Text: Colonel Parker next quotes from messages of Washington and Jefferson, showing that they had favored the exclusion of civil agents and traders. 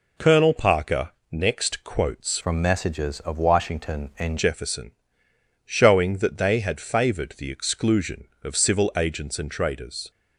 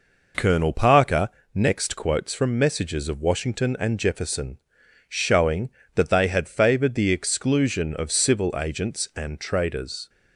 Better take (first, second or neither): second